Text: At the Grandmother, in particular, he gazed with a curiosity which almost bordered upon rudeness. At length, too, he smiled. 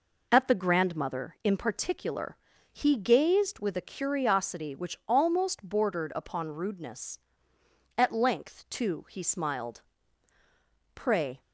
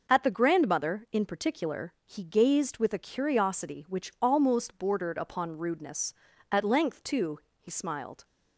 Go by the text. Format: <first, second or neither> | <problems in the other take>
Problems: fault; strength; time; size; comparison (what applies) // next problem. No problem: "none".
second | goes on to say "Pray"; slight; from 10.9 s on; 0.46 s long